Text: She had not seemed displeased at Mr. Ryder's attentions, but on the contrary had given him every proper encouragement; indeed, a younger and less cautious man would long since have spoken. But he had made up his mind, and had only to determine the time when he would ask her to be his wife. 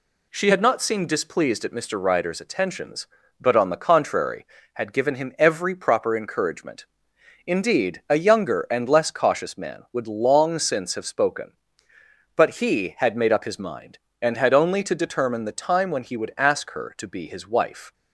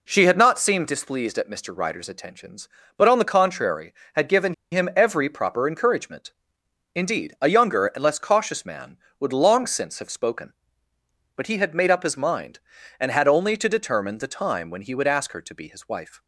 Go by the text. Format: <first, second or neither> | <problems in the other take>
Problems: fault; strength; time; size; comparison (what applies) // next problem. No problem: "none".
first | pauses between "given" and "him"; slight; at 4.5 s; 0.17 s long